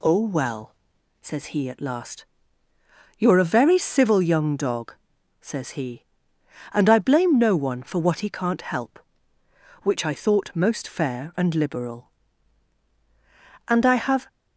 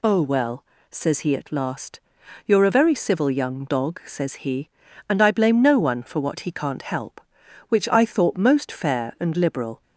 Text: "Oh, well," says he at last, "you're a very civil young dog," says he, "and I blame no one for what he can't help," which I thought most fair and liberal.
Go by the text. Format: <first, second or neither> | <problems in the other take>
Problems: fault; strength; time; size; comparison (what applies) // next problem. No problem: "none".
second | goes on to say "And I have"; from 13.6 s on; 0.60 s long